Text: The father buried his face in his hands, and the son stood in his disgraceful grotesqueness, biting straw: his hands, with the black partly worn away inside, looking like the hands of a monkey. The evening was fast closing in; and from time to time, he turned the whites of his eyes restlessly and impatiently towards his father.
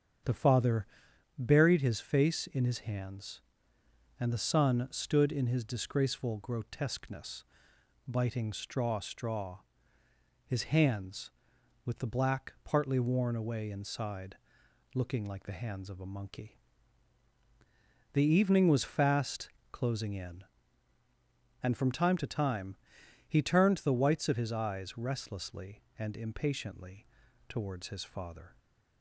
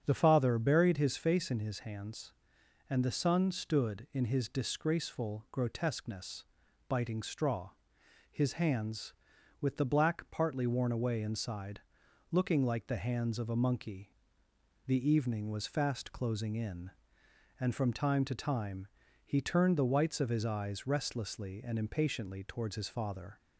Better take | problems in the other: second | starts louder than the rest; strong; until 1.7 s; 7.5 dB; strong in the second // pauses between "father" and "buried"; noticeable; at 0.8 s; 0.50 s long // says "straw" twice; at 9.0 s // pauses between "fast" and "closing"; slight; at 19.5 s; 0.22 s long // pauses between "impatiently" and "towards"; at 27.0 s; 0.42 s long

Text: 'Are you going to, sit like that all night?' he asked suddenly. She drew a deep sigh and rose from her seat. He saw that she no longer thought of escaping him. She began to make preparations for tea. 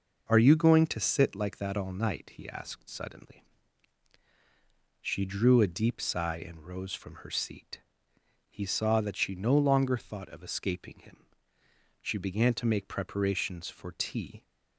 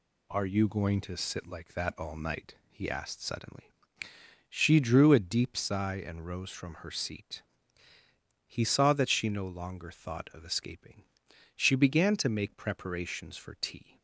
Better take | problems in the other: first | skips "him"; at 11.2 s

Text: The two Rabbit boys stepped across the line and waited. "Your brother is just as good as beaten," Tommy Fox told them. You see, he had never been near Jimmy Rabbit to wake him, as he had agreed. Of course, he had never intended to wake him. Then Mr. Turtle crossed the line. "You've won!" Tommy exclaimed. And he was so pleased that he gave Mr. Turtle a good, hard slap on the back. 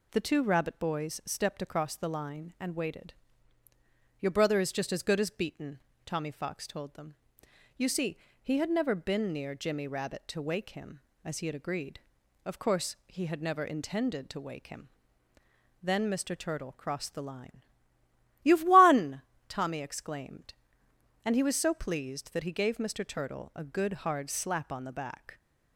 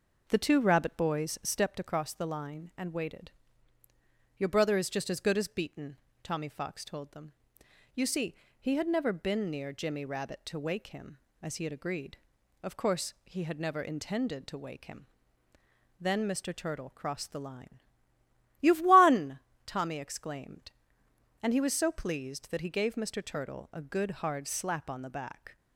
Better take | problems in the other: first | starts louder than the rest; noticeable; until 1.7 s; 5 dB

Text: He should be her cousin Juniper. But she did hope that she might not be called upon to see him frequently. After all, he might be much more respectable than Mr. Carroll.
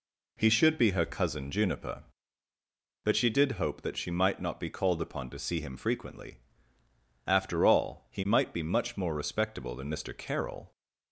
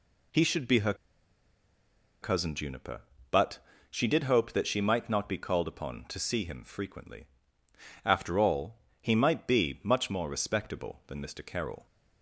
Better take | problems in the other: first | pauses between "her" and "cousin"; strong; at 0.9 s; 1.2 s long // pauses between "But" and "she"; slight; at 3.5 s; 0.32 s long

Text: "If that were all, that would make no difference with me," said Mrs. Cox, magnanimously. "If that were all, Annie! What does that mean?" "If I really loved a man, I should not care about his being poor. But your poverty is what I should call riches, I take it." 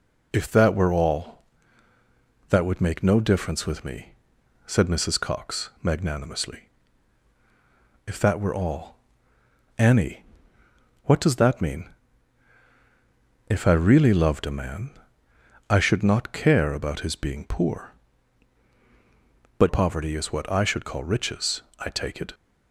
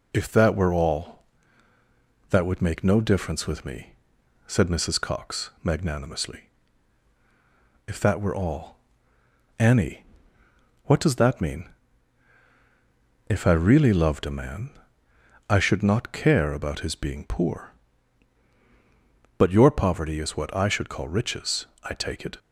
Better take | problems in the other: second | skips "your"; at 19.6 s

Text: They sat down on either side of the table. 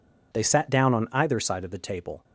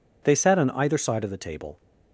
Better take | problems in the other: first | skips "down"; at 0.5 s

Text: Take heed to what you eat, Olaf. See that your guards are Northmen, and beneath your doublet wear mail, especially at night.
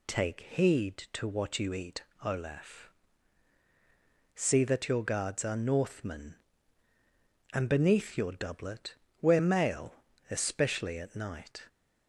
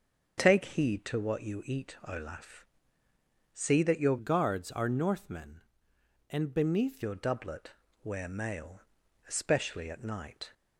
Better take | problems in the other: first | starts louder than the rest; until 1.4 s; 7 dB // changes voice from "guards" to "beneath"; from 4.1 to 7.0 s; 2.9 s long // pauses between "doublet" and "wear"; slight; at 7.7 s; 0.30 s long; slight in the first

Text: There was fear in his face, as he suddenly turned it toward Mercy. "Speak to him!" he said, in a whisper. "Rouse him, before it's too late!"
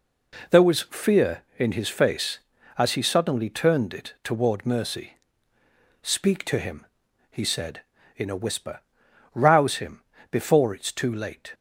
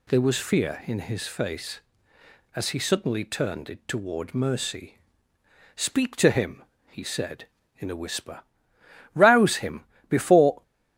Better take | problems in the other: first | stops before "it's too late"; at 10.6 s

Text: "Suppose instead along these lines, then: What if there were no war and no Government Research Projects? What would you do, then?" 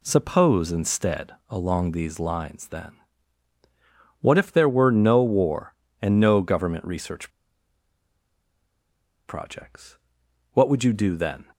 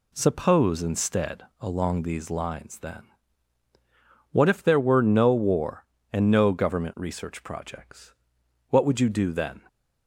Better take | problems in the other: second | pauses between "instead" and "along"; slight; at 1.3 s; 0.16 s long; slight in the second // pauses between "Research" and "Projects"; strong; at 7.2 s; 1.9 s long

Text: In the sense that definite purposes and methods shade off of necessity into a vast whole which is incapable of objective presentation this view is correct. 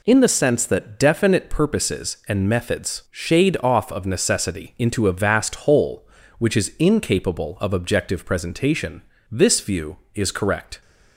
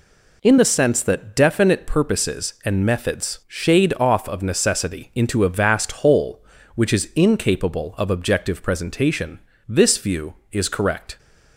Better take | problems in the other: neither | pauses between "presentation" and "this"; slight; the same in both

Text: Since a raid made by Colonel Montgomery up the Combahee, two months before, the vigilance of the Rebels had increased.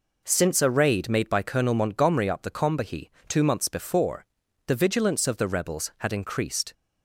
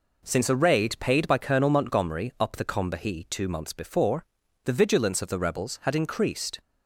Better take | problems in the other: first | says "paid" for "made"; at 0.9 s

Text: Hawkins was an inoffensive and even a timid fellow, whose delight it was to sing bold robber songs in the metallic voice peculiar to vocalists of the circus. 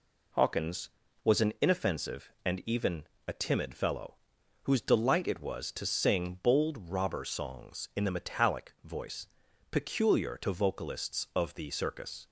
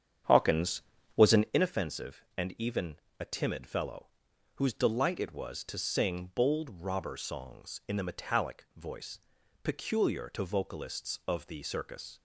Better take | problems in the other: first | starts louder than the rest; strong; until 1.6 s; 8.5 dB // pauses between "even" and "a"; slight; at 2.9 s; 0.18 s long; slight in the first // pauses between "voice" and "peculiar"; noticeable; at 9.1 s; 0.46 s long; noticeable in the first

